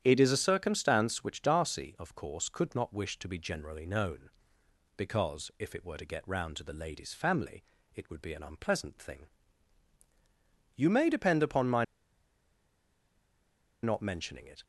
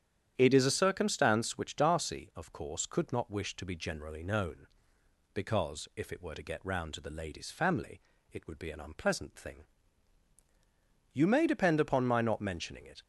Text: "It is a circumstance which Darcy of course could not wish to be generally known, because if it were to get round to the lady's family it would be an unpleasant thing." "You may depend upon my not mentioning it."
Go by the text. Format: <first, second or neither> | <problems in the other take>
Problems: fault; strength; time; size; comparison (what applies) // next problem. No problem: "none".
second | starts louder than the rest; strong; until 1.0 s; 9.5 dB; strong in the second // pauses between "family" and "it"; slight; at 7.6 s; 0.30 s long; slight in the second // pauses between "my" and "not"; strong; at 11.8 s; 1.9 s long